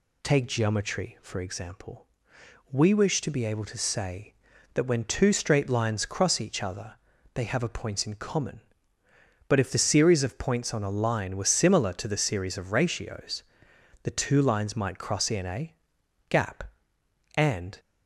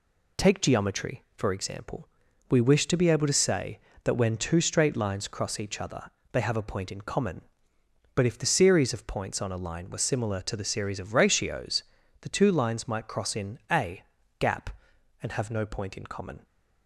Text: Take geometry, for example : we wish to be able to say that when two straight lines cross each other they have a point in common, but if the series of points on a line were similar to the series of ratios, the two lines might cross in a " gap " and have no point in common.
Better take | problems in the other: second | pauses between "other" and "they"; at 6.9 s; 0.40 s long; slight in the second // stops before "have no point in common"; at 17.7 s

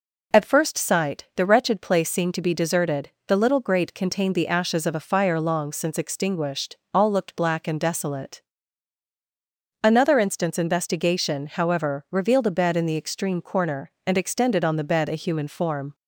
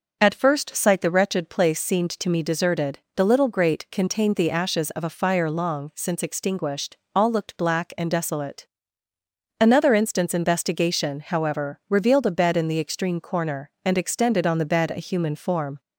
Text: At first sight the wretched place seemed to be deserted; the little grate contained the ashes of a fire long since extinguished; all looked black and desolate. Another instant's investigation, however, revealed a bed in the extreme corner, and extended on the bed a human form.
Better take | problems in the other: first | says "me" for "be"; at 2.2 s

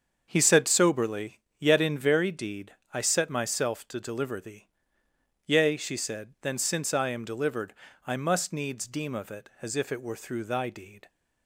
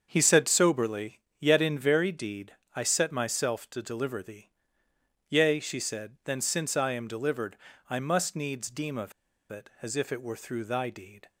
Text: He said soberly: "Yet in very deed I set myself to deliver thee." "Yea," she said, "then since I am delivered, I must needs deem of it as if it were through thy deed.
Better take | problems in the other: first | starts louder than the rest; until 1.1 s; 7 dB; also in the first // pauses between "deed" and "I"; slight; at 2.5 s; 0.18 s long; slight in the first // pauses between "of" and "it"; at 9.1 s; 0.37 s long

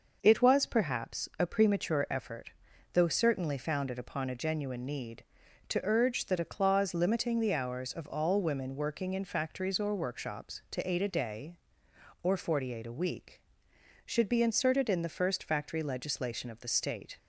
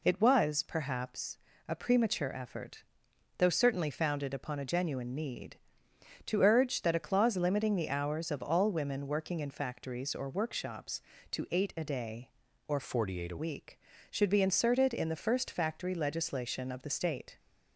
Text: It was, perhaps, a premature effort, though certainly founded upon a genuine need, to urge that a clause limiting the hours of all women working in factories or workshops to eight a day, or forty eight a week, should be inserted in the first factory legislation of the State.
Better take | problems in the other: first | changes voice from "forty" to "a"; from 12.8 to 13.3 s; 0.5 s long

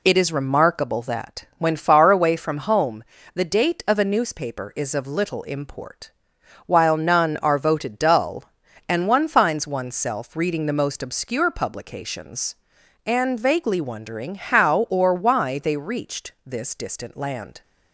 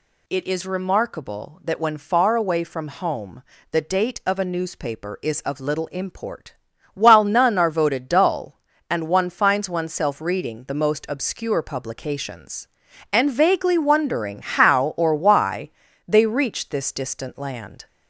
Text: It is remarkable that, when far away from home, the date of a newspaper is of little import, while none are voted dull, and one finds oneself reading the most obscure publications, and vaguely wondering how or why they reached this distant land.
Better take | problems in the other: first | gets louder; slight; throughout; 3 dB // pauses between "why" and "they"; at 15.6 s; 0.38 s long

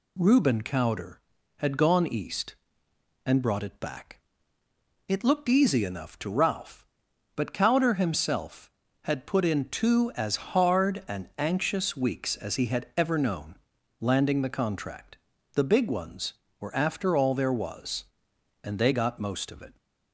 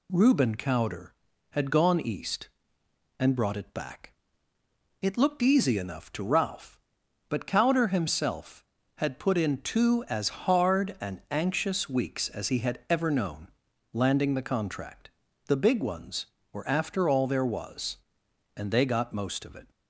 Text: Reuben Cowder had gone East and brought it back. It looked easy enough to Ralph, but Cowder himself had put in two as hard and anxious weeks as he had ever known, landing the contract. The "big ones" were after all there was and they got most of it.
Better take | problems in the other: neither | none

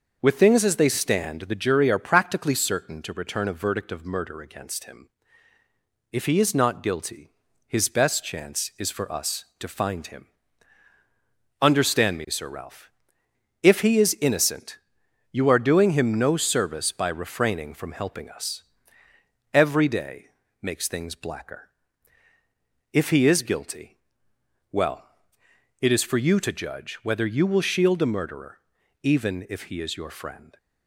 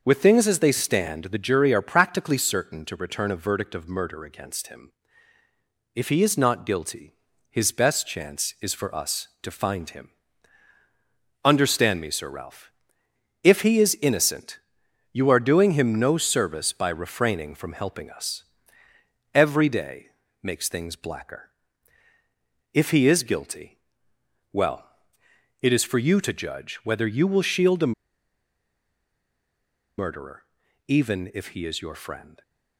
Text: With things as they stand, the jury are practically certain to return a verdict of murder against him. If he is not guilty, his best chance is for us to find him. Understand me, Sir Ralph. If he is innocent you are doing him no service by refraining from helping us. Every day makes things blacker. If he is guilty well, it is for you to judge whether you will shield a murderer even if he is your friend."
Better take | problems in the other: first | pauses between "innocent" and "you"; noticeable; at 14.5 s; 0.56 s long; noticeable in the first // pauses between "day" and "makes"; slight; at 20.0 s; 0.36 s long; slight in the first // pauses between "guilty" and "well"; noticeable; at 23.7 s; 0.78 s long; noticeable in the first // pauses between "a" and "murderer"; strong; at 27.9 s; 2.0 s long // pauses between "murderer" and "even"; at 30.4 s; 0.44 s long; also in the first

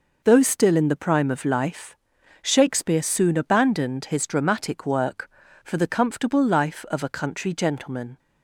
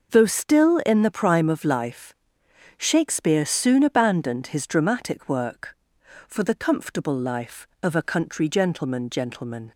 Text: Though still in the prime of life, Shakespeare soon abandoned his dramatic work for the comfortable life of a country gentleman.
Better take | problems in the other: first | says "gentleman" twice; at 9.0 s

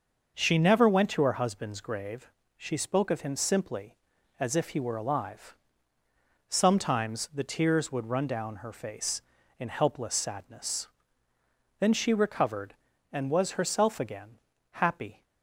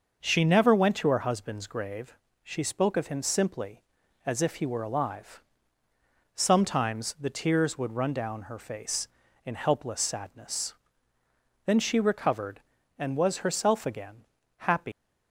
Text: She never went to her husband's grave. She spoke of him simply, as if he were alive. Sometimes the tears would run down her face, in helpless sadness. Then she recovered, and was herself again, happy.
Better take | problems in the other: first | starts louder than the rest; until 1.2 s; 6 dB; also in the first // leaves "happy" unfinished; at 14.9 s; 175 ms

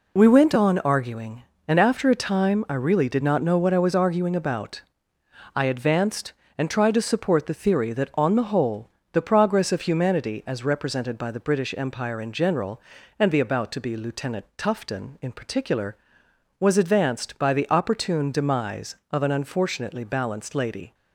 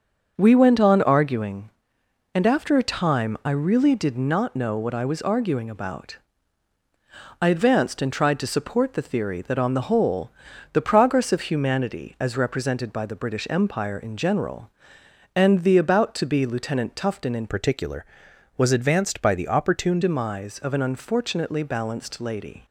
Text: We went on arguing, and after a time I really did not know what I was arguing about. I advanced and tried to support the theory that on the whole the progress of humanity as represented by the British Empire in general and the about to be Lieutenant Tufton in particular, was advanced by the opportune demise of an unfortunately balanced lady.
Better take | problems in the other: first | starts louder than the rest; until 1.3 s; 6.5 dB // pauses between "whole" and "the"; at 10.3 s; 0.40 s long; slight in the first // changes voice from "particular" to "opportune"; from 17.4 to 20.0 s; 2.6 s long

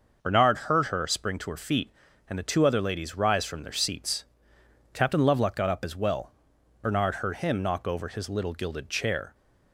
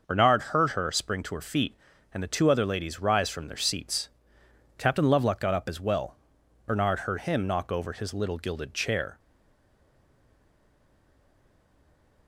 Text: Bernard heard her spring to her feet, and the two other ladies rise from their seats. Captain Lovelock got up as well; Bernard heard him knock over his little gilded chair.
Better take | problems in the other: first | starts louder than the rest; noticeable; until 1.0 s; 6 dB; noticeable in the first // stays silent after the last word; strong; from 9.1 s on; 3.1 s long

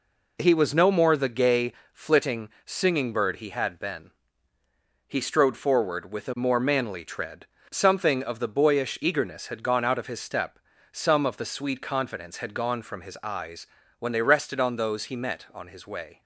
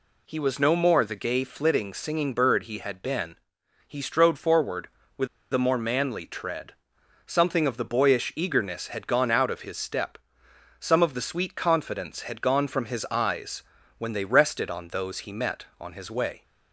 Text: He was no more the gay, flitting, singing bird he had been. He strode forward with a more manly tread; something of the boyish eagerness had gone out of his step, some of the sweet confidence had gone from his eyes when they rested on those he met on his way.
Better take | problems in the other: first | pauses between "with" and "a"; slight; at 5.2 s; 0.26 s long // pauses between "eyes" and "when"; slight; at 13.6 s; 0.36 s long; slight in the first

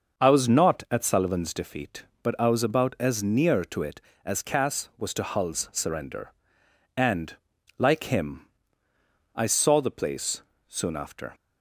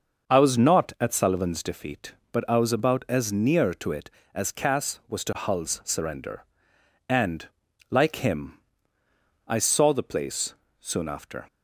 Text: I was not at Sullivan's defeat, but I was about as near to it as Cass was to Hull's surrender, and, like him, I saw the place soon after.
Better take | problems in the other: neither | starts louder than the rest; the same in both // pauses between "place" and "soon"; slight; the same in both

